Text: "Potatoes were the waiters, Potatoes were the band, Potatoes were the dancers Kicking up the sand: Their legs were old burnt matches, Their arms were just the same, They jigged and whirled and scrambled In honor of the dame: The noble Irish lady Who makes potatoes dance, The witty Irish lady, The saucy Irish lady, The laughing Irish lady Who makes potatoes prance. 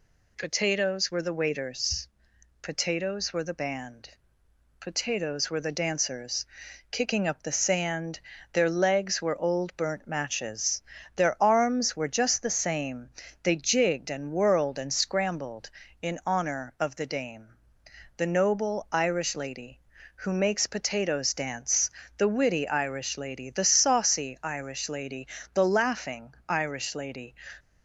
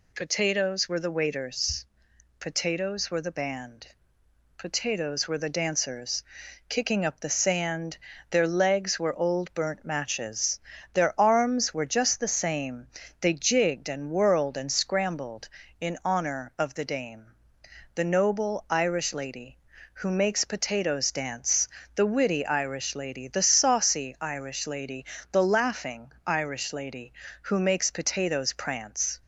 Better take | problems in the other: second | pauses between "dancers" and "Kicking"; noticeable; at 6.4 s; 0.46 s long; noticeable in the second // pauses between "laughing" and "Irish"; slight; at 26.3 s; 0.16 s long; slight in the second // stops before "Who makes potatoes prance"; at 27.5 s

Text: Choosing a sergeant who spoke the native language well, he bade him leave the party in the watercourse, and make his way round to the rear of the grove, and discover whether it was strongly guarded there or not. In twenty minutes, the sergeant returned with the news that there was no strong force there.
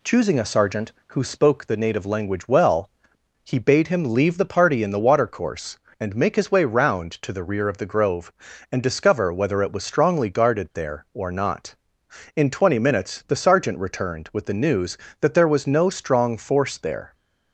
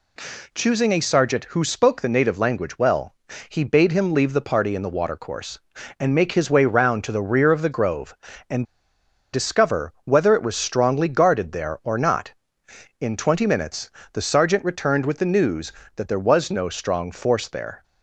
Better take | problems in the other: first | pauses between "and" and "discover"; noticeable; at 8.6 s; 0.68 s long

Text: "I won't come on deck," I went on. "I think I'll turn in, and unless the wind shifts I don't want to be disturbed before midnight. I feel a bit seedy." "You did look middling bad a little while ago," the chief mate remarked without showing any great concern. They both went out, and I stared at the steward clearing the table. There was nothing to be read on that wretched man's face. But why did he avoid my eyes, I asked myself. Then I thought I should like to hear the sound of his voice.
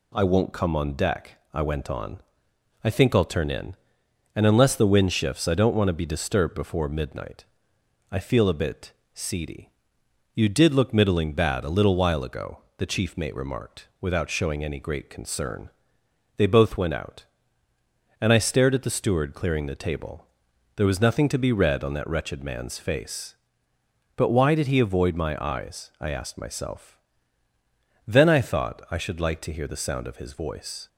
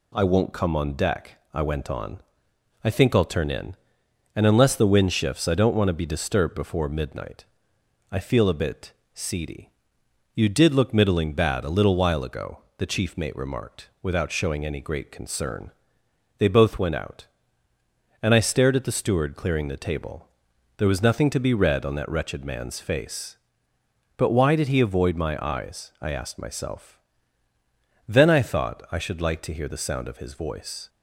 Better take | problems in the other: neither | pauses between "bit" and "seedy"; slight; the same in both

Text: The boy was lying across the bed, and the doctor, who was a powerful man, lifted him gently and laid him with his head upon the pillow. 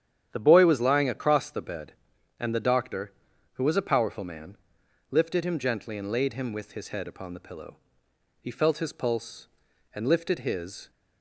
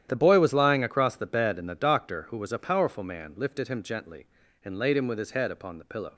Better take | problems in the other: second | starts louder than the rest; strong; until 1.3 s; 9.5 dB; strong in the second // goes on to say "He felt his pulse and lifted his"; strong; from 8.3 s on; 2.5 s long

